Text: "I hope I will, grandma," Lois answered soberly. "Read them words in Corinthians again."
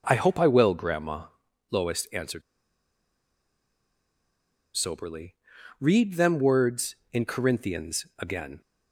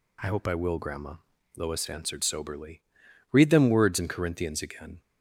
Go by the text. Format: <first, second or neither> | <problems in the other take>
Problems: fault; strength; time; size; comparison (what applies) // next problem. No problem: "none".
second | pauses between "answered" and "soberly"; strong; at 2.4 s; 2.3 s long